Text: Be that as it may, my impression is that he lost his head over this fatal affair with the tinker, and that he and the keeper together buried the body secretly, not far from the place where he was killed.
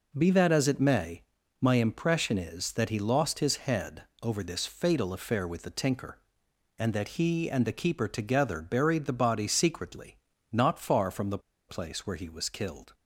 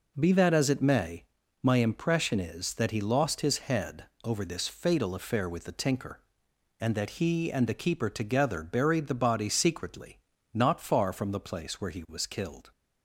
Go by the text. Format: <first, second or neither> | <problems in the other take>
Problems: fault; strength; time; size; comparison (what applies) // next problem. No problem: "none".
second | pauses between "head" and "over"; slight; at 4.0 s; 0.20 s long; slight in the second // pauses between "the" and "place"; slight; at 11.3 s; 0.30 s long